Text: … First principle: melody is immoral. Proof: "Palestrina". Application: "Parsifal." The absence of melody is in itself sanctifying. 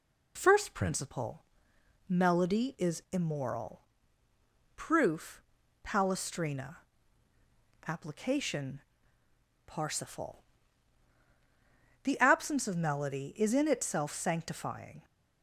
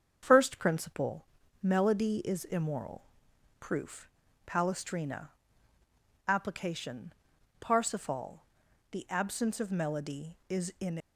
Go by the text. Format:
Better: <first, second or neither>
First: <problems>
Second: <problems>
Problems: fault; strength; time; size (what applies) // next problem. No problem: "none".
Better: first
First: none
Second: starts louder than the rest; strong; until 1.2 s; 7 dB // stops before "itself sanctifying"; at 10.9 s